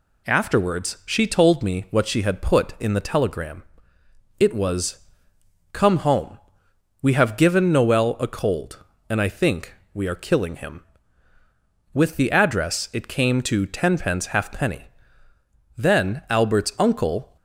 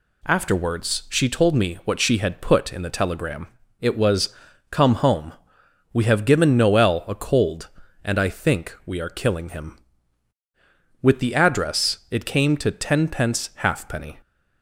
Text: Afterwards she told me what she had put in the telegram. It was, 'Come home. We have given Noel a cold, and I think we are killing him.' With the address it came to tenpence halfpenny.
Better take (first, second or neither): second